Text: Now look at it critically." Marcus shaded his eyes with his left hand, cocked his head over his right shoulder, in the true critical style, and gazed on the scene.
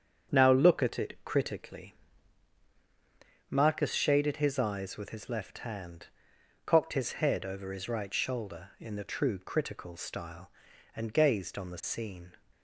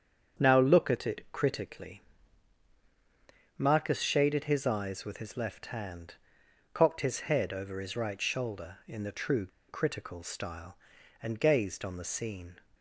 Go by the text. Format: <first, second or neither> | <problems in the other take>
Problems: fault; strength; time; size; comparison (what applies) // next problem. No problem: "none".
first | starts louder than the rest; strong; until 1.5 s; 8 dB; strong in the first // pauses between "true" and "critical"; slight; at 9.4 s; 0.21 s long